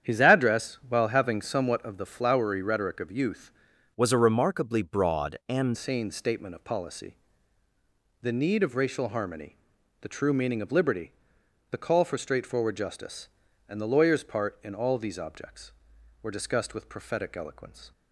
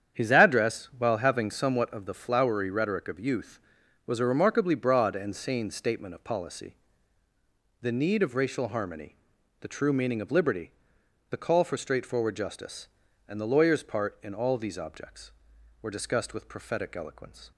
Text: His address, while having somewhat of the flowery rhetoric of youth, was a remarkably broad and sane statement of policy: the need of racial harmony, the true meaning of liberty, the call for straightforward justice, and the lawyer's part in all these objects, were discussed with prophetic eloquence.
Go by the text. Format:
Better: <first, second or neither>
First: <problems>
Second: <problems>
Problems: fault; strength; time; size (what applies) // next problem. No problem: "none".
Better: second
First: starts louder than the rest; strong; until 1.1 s; 9 dB // changes voice from "was" to "and"; from 3.9 to 5.7 s; 1.8 s long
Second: starts louder than the rest; strong; until 1.2 s; 8.5 dB